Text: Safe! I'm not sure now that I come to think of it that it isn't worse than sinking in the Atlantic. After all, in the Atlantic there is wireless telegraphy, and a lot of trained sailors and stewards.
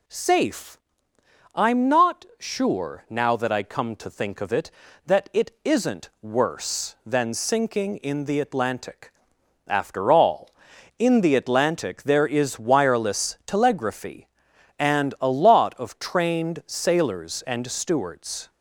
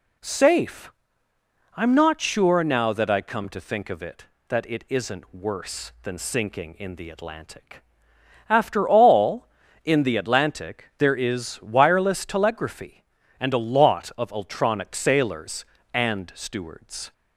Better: first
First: none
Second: says "ultronic" for "trained"; at 14.3 s

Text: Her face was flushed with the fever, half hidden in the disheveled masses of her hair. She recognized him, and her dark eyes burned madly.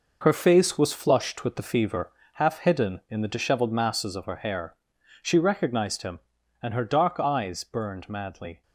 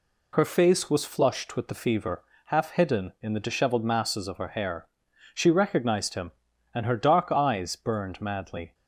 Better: second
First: gets quieter; strong; throughout; 8.5 dB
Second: none

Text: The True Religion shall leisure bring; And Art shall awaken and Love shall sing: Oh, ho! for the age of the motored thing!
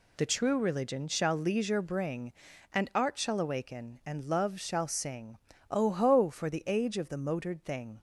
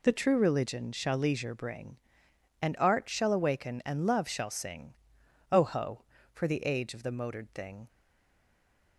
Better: first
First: none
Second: stays silent after the last word; from 7.8 s on; 1.1 s long

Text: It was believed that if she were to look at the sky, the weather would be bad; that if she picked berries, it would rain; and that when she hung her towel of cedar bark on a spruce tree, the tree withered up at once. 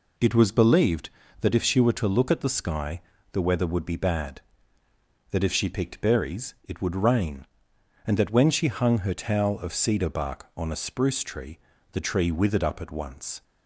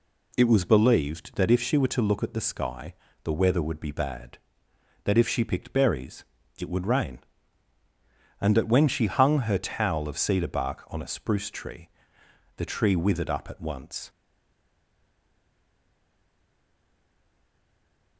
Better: first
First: none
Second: stays silent after the last word; strong; from 14.0 s on; 4.1 s long

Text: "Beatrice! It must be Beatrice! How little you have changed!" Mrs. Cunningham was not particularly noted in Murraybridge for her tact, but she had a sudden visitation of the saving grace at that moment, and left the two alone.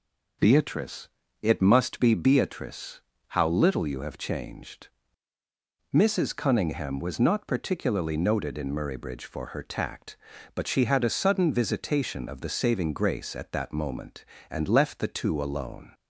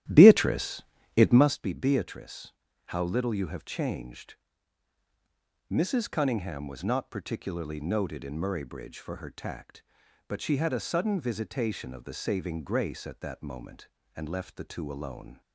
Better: first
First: none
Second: starts louder than the rest; strong; until 1.6 s; 13 dB

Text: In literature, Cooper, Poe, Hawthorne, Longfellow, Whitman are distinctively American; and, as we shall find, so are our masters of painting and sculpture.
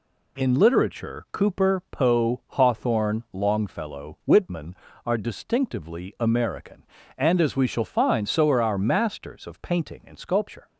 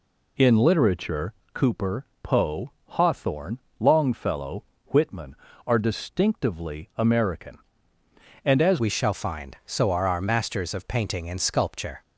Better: first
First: none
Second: changes voice at "we"; from 8.7 s on; 3.3 s long

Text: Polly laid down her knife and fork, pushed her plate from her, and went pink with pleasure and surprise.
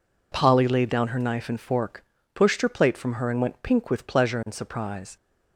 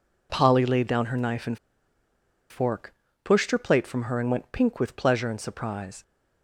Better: first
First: none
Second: pauses between "and" and "fork"; noticeable; at 1.5 s; 0.91 s long

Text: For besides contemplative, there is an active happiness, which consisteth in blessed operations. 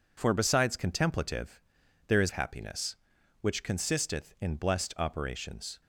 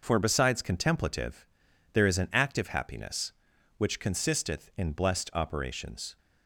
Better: second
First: skips "an active"; at 2.2 s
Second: none

